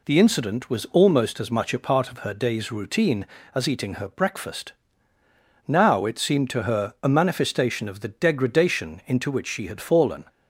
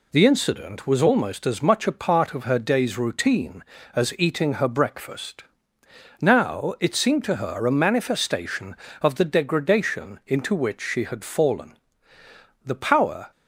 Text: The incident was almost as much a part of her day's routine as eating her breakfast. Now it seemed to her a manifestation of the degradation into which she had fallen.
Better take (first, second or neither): first